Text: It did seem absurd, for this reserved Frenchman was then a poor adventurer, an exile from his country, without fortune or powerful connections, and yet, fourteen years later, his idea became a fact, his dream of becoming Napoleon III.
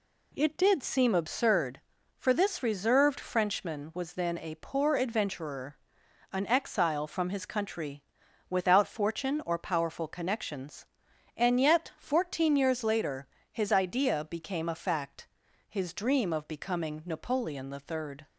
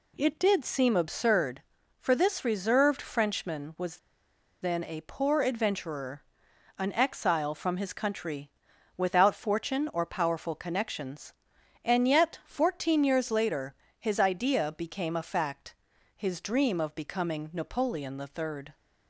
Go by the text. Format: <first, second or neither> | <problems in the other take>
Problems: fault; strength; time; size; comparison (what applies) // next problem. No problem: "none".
first | pauses between "was" and "then"; noticeable; at 3.9 s; 0.65 s long